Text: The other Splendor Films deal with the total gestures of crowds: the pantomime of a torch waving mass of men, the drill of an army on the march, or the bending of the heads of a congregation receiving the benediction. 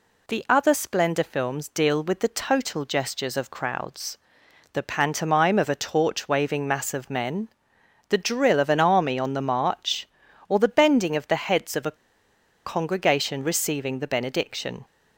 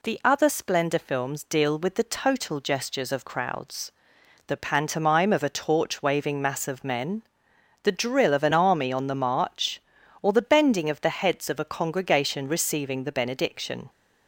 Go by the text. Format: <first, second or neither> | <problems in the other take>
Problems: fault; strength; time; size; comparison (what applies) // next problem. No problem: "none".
second | pauses between "a" and "congregation"; noticeable; at 11.9 s; 0.71 s long